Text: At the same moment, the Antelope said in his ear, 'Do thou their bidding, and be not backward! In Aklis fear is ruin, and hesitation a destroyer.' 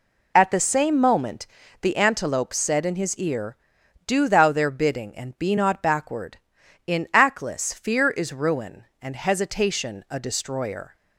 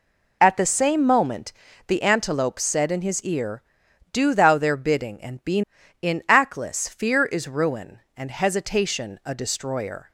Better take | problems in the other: first | skips "not backward"; at 5.8 s

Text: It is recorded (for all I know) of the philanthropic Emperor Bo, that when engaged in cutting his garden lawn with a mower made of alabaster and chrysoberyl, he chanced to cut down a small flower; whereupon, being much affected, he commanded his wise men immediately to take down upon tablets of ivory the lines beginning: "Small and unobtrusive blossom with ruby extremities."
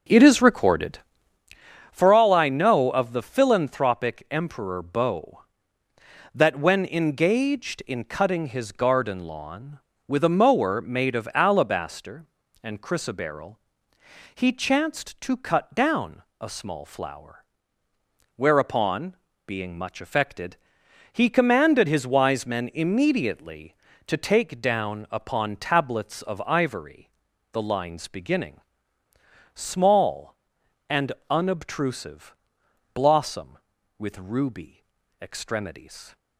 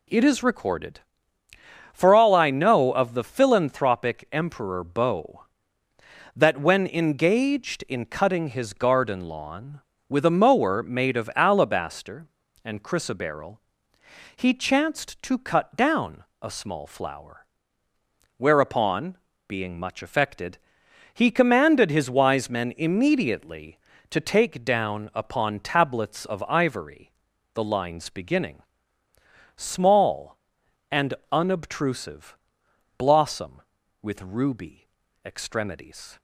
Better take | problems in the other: second | starts louder than the rest; until 1.6 s; 6.5 dB // pauses between "down" and "a"; slight; at 16.2 s; 0.18 s long; slight in the second // pauses between "ivory" and "the"; at 27.0 s; 0.44 s long; also in the second // pauses between "and" and "unobtrusive"; slight; at 31.1 s; 0.16 s long; slight in the second // pauses between "unobtrusive" and "blossom"; noticeable; at 32.3 s; 0.60 s long; noticeable in the second // pauses between "ruby" and "extremities"; at 34.8 s; 0.40 s long; also in the second

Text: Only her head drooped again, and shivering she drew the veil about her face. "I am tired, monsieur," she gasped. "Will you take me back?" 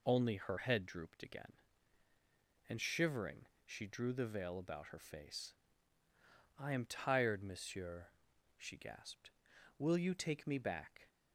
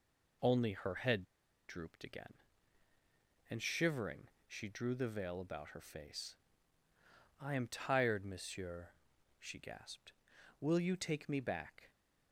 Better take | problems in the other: first | pauses between "head" and "drooped"; at 1.2 s; 0.44 s long // pauses between "shivering" and "she"; slight; at 4.2 s; 0.18 s long; slight in the first

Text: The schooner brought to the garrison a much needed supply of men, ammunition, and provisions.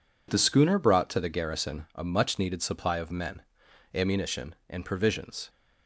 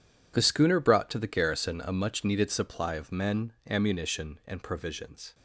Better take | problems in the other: neither | none

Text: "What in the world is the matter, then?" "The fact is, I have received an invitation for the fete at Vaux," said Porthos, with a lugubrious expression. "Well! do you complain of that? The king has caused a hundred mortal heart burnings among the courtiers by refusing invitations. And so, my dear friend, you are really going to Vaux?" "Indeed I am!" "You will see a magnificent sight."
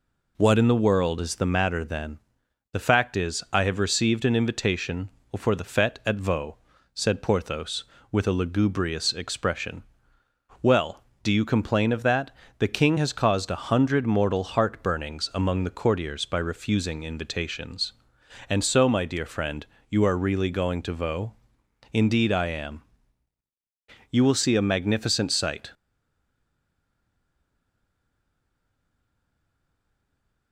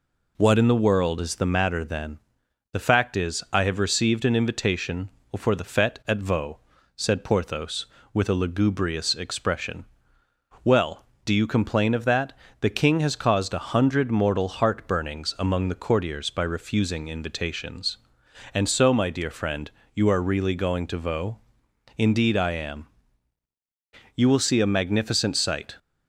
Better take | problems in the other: second | stays silent after the last word; strong; from 25.7 s on; 4.8 s long

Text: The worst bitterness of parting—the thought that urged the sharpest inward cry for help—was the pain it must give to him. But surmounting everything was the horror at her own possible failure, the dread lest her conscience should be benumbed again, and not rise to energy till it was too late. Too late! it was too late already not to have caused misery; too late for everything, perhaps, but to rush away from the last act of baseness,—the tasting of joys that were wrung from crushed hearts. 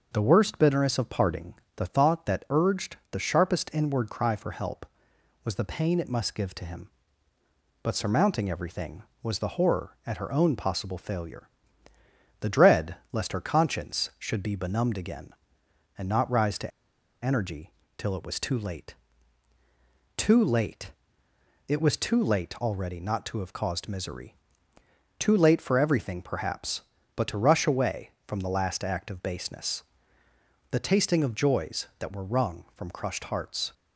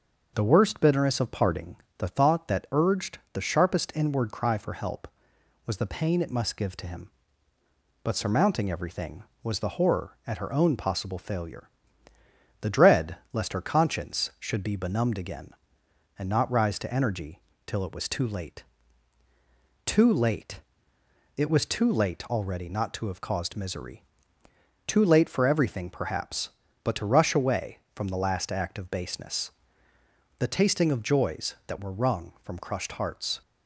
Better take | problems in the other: second | starts louder than the rest; noticeable; until 1.1 s; 6 dB; noticeable in the second // pauses between "dread" and "lest"; slight; at 12.9 s; 0.18 s long; slight in the second // pauses between "to" and "energy"; noticeable; at 16.7 s; 0.54 s long // pauses between "energy" and "till"; slight; at 17.7 s; 0.26 s long; slight in the second

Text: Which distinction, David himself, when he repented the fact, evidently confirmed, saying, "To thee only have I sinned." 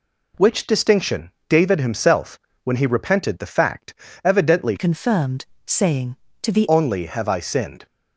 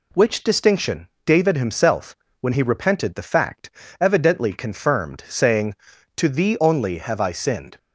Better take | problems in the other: second | changes voice from "confirmed" to "thee"; from 4.7 to 6.6 s; 1.9 s long

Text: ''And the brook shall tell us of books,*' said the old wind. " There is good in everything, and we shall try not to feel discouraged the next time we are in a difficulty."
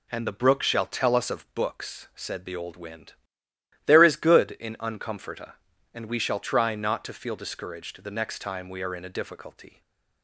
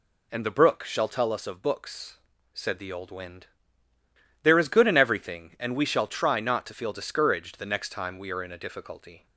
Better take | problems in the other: second | says "uncomforta" for "everything"; at 4.7 s // stays silent after the last word; slight; from 9.6 s on; 0.6 s long

